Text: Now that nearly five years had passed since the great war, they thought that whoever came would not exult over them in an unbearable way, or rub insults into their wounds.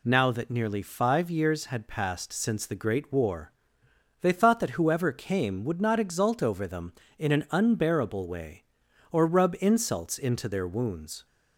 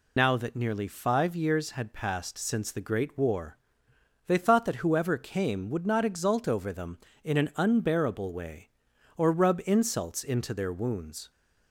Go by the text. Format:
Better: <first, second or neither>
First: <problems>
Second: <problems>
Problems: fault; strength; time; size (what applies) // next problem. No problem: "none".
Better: first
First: none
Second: loses the start of "Now"; at 0.1 s; 65 ms